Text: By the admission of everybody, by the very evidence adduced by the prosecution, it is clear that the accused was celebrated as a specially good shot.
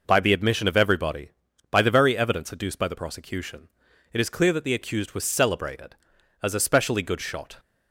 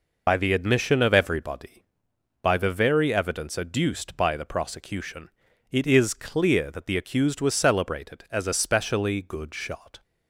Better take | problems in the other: first | loses the start of "By"; at 0.2 s; 45 ms

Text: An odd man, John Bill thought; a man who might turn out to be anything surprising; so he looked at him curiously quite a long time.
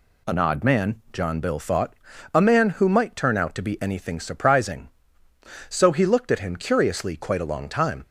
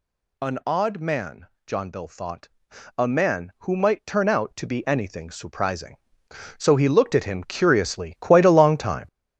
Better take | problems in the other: first | gets louder; strong; throughout; 7 dB

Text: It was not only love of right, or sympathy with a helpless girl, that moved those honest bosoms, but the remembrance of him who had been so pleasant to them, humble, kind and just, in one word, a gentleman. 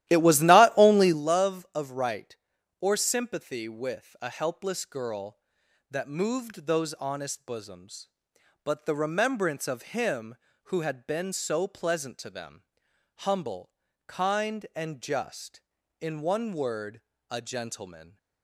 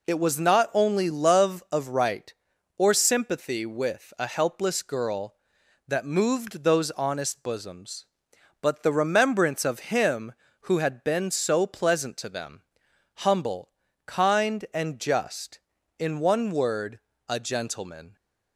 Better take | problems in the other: second | starts louder than the rest; strong; until 1.2 s; 14 dB

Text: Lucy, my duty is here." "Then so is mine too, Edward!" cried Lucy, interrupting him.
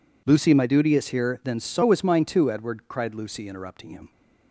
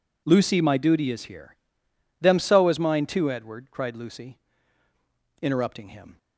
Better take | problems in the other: first | says "Them" for "Then"; at 2.1 s

